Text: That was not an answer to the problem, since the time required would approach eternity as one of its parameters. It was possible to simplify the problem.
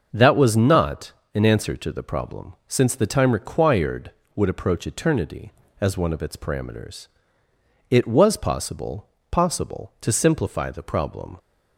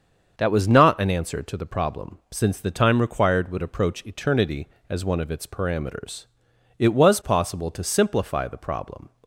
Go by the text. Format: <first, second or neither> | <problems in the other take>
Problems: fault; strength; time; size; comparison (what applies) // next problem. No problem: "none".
second | starts louder than the rest; noticeable; until 1.1 s; 6 dB; also in the second // pauses between "not" and "an"; slight; at 1.1 s; 0.22 s long // says "possible" twice; at 9.3 s